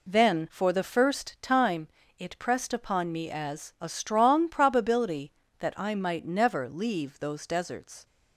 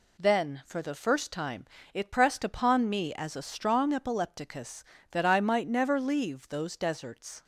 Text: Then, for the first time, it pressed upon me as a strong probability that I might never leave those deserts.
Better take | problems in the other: first | says "epilepticus" for "probability"; at 3.9 s

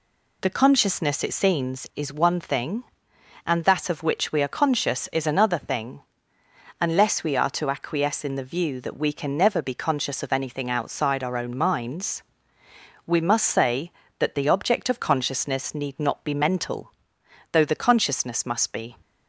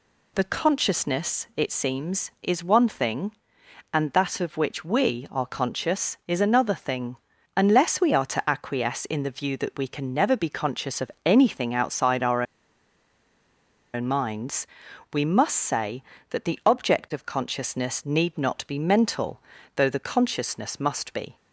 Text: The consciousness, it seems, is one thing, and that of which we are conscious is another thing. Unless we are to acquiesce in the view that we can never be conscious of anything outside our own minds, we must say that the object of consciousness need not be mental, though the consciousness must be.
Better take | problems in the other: first | pauses between "of" and "anything"; slight; at 11.0 s; 0.16 s long // pauses between "our" and "own"; strong; at 12.4 s; 1.5 s long

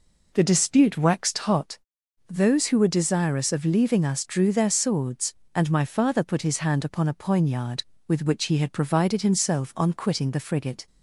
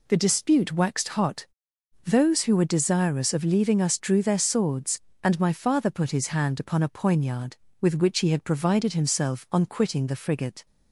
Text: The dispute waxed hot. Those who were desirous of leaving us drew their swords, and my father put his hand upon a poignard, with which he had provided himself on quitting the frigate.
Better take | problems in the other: second | starts louder than the rest; noticeable; until 1.7 s; 4.5 dB

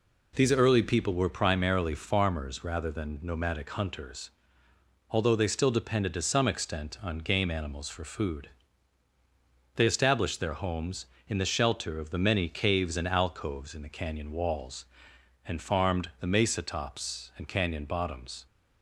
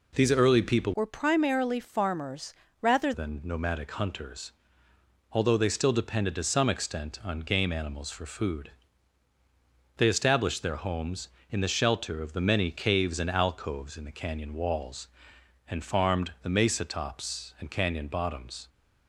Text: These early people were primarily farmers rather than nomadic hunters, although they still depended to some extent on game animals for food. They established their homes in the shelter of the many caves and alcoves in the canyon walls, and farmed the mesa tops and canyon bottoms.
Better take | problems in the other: first | changes voice from "were" to "rather"; from 0.9 to 3.1 s; 2.2 s long // pauses between "farmers" and "rather"; slight; at 2.5 s; 0.28 s long

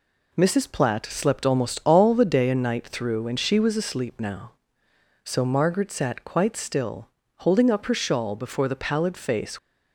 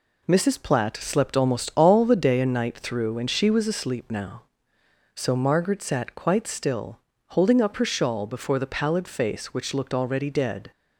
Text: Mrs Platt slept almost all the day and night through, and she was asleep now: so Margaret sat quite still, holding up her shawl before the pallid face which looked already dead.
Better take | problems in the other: second | stops before "which looked already dead"; at 9.5 s

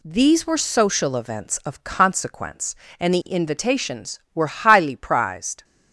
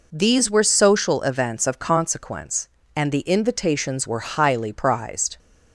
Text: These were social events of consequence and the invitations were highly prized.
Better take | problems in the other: neither | none

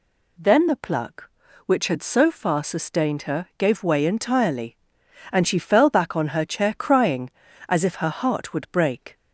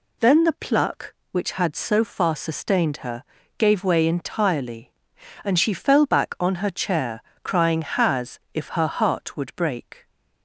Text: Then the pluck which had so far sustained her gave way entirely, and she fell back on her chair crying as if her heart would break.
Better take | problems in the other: first | pauses between "her" and "gave"; slight; at 3.2 s; 0.34 s long // pauses between "chair" and "crying"; slight; at 7.2 s; 0.22 s long // says "has" for "as"; at 7.8 s

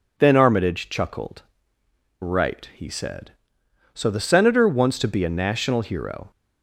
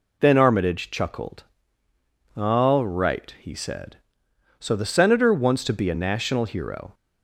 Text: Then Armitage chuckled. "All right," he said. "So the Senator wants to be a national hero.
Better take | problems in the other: second | skips "All"; at 1.8 s

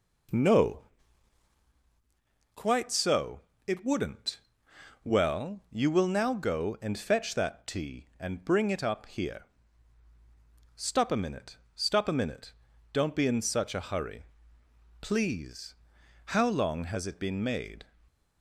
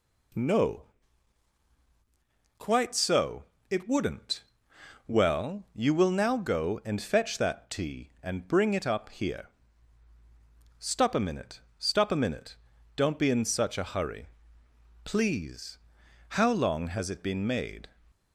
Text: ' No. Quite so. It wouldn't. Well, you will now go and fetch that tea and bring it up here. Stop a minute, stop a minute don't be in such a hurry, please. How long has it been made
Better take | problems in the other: second | starts louder than the rest; noticeable; until 1.7 s; 4.5 dB // pauses between "minute" and "don't"; at 12.5 s; 0.40 s long; also in the second // stays silent after the last word; slight; from 17.8 s on; 0.6 s long

